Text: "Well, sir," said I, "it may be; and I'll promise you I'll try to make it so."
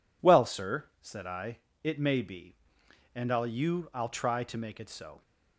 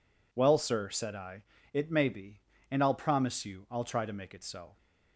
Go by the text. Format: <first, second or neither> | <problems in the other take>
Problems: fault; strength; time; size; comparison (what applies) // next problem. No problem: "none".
second | skips "promise"; at 3.4 s